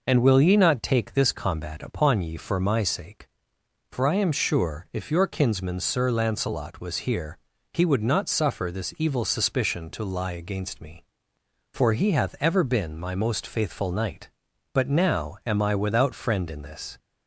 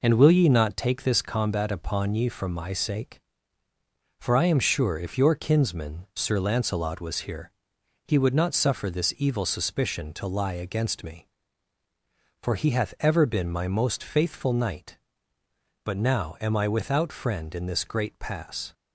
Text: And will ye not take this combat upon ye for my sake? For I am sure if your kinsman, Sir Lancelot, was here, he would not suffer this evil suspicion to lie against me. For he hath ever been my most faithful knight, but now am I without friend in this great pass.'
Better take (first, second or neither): second